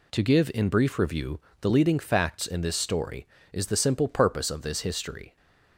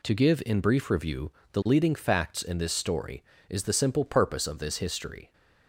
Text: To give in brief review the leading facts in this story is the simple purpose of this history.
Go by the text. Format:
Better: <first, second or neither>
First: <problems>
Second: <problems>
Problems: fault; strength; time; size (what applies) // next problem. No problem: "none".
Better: neither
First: pauses between "review" and "the"; slight; at 1.3 s; 0.20 s long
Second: pauses between "review" and "the"; slight; at 1.3 s; 0.20 s long